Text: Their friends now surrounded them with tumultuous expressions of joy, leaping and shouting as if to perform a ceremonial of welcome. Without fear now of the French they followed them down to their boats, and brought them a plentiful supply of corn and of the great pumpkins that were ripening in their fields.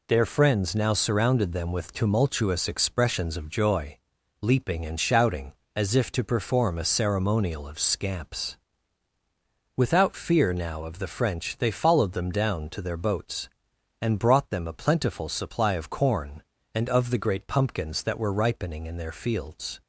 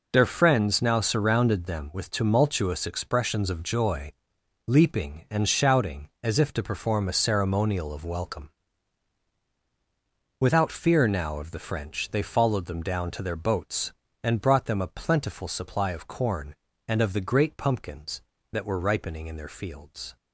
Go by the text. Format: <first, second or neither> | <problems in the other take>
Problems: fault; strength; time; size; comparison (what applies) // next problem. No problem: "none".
second | says "scamps" for "welcome"; at 7.7 s